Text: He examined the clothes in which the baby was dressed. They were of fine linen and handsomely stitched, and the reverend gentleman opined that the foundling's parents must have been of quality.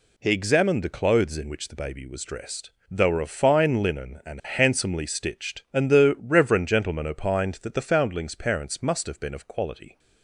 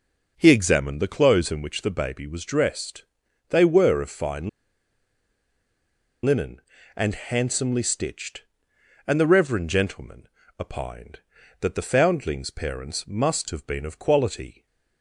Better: first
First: none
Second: pauses between "fine" and "linen"; strong; at 4.4 s; 1.7 s long // pauses between "gentleman" and "opined"; slight; at 10.2 s; 0.30 s long

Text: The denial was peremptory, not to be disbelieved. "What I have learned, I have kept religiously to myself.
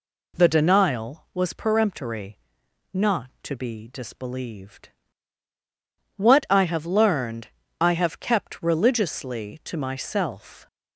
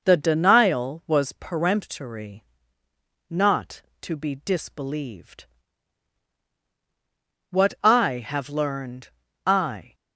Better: first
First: none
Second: stops before "have kept religiously to myself"; at 9.9 s

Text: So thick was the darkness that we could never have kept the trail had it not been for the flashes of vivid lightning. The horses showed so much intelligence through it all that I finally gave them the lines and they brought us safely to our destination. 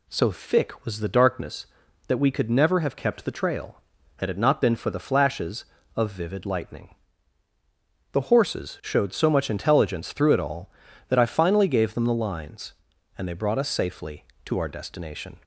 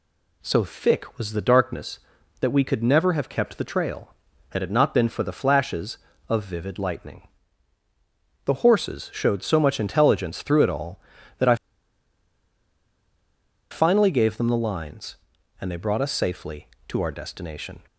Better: first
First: none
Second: pauses between "I" and "finally"; strong; at 11.5 s; 2.1 s long

